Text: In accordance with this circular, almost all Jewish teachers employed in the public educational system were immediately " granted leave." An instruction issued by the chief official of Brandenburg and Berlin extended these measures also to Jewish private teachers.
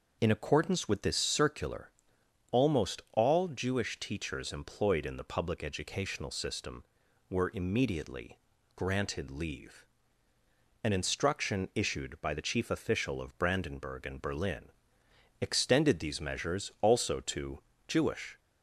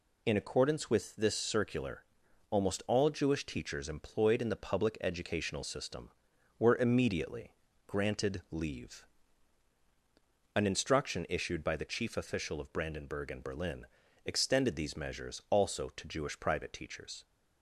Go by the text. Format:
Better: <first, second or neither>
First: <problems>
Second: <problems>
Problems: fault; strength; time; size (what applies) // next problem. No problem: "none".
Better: second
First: pauses between "Berlin" and "extended"; noticeable; at 14.7 s; 0.70 s long // pauses between "to" and "Jewish"; slight; at 17.6 s; 0.26 s long // stops before "private teachers"; at 18.3 s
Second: pauses between "Berlin" and "extended"; at 13.8 s; 0.38 s long